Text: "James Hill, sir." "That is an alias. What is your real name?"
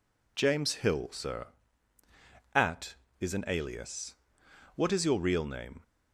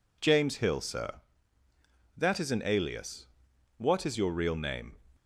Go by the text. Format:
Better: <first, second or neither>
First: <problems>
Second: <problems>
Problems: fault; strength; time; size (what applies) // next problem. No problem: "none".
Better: second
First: says "At" for "That"; at 2.5 s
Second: none